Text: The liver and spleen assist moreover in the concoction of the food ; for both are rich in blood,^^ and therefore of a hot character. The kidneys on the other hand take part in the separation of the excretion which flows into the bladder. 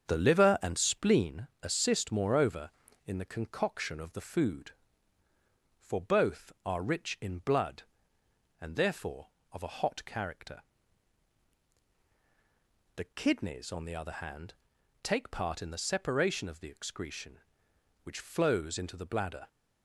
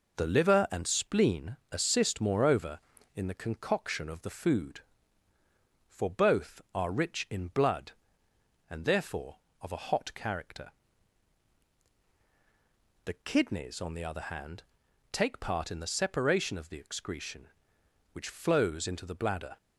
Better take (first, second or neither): second